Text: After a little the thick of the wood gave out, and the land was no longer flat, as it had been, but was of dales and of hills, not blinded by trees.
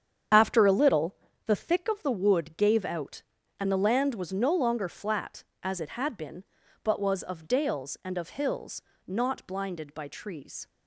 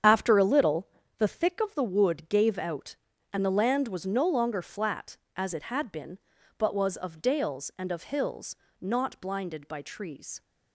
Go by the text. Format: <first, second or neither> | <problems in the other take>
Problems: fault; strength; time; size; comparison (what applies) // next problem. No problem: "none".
neither | starts louder than the rest; strong; the same in both // pauses between "little" and "the"; slight; the same in both